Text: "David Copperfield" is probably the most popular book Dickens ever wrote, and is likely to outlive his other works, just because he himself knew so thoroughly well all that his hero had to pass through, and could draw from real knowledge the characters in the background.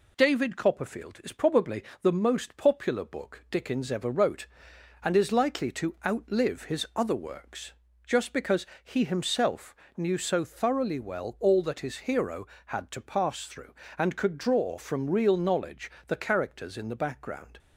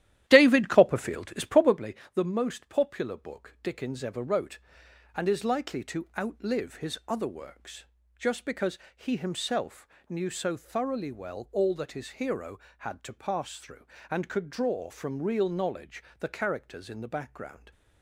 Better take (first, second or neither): first